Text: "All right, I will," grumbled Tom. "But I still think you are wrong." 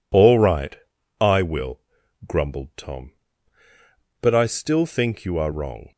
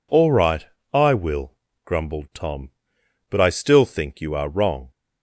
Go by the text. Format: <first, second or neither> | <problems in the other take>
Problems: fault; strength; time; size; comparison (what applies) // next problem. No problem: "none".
neither | none